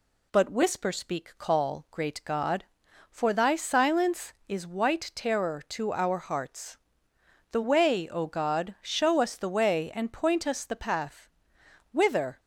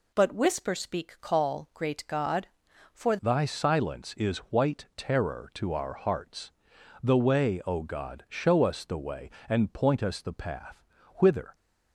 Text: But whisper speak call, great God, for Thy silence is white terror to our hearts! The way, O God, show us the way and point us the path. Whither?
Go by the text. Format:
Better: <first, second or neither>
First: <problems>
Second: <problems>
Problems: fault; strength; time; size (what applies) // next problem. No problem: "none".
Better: first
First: none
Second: changes voice at "Thy"; from 3.2 s on; 8.3 s long